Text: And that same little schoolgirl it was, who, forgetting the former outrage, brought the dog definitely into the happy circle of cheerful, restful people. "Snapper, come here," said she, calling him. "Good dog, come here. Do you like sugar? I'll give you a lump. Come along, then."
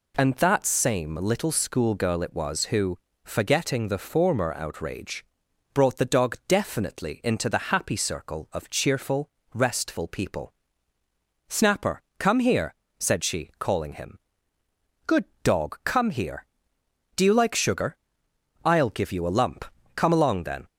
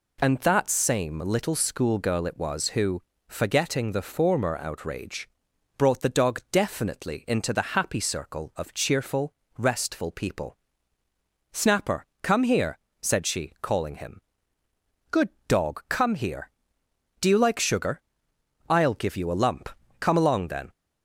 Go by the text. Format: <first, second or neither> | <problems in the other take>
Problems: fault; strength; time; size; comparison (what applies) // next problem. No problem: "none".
neither | pauses between "Good" and "dog"; slight; the same in both